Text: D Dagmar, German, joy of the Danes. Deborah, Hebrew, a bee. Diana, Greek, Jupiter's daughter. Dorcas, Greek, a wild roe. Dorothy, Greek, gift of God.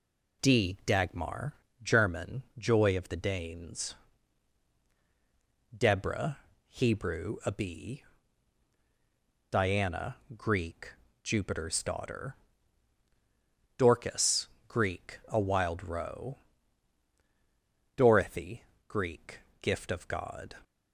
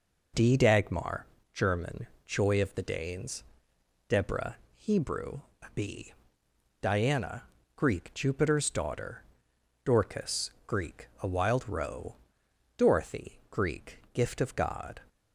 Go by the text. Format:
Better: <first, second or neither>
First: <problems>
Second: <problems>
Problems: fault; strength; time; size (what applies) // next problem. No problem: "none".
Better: neither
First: none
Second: none